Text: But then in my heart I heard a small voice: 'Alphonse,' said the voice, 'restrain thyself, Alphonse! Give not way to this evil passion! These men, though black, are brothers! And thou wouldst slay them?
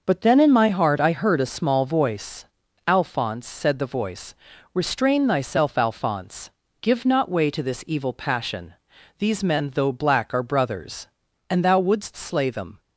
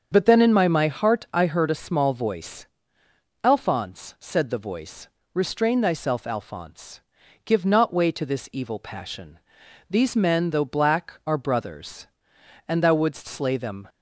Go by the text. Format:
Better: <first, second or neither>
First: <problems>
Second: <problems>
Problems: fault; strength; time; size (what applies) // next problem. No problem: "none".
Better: first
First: none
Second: starts louder than the rest; until 1.1 s; 7 dB // says "my" twice; at 0.6 s